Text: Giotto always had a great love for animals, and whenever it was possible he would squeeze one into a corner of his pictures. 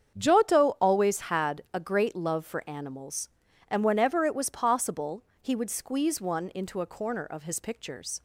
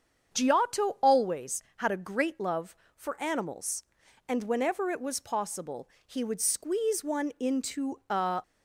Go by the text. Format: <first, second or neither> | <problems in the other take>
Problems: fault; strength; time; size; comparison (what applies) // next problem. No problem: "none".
first | starts louder than the rest; strong; until 1.3 s; 7.5 dB; strong in the first // pauses between "possible" and "he"; slight; at 5.8 s; 0.18 s long; slight in the first // stops before "corner of his pictures"; at 8.4 s